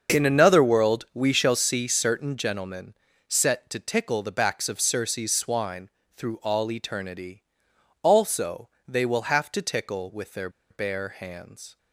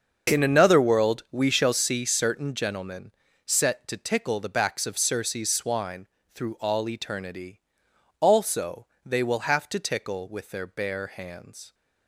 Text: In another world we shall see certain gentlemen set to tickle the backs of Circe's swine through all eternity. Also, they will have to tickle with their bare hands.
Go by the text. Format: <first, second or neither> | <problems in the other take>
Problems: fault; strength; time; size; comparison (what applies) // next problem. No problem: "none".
second | starts louder than the rest; until 1.2 s; 6.5 dB; also in the second // pauses between "gentlemen" and "set"; slight; at 2.9 s; 0.34 s long; slight in the second // pauses between "swine" and "through"; slight; at 5.8 s; 0.28 s long; slight in the second // pauses between "their" and "bare"; slight; at 10.4 s; 0.21 s long